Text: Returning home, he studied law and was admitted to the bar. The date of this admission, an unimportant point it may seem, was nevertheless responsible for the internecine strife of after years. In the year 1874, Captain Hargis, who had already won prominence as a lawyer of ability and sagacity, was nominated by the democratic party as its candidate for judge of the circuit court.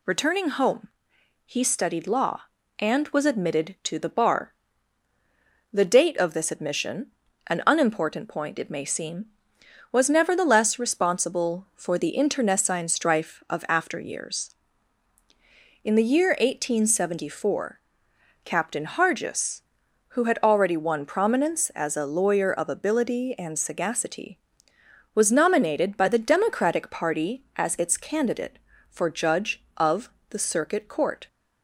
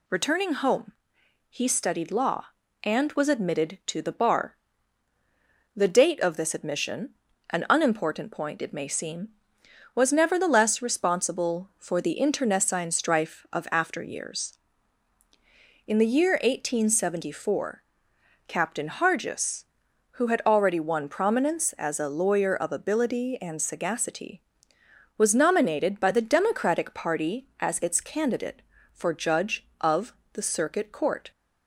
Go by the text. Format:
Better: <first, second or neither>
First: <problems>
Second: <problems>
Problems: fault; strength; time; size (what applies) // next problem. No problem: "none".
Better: neither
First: pauses between "of" and "the"; slight; at 30.0 s; 0.20 s long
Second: pauses between "of" and "the"; slight; at 30.1 s; 0.20 s long